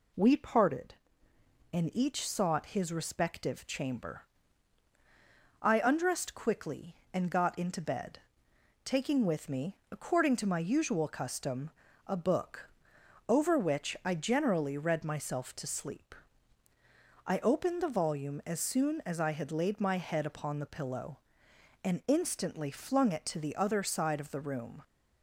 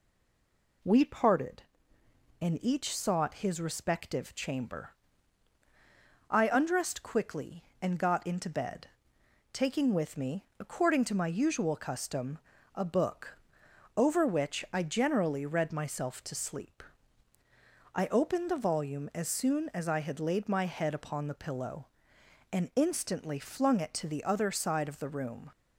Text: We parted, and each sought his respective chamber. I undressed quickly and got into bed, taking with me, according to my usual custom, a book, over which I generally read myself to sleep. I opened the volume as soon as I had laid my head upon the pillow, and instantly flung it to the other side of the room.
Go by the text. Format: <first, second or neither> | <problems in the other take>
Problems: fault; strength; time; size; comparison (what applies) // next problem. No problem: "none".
first | stays silent before the first word; slight; until 0.8 s; 0.8 s long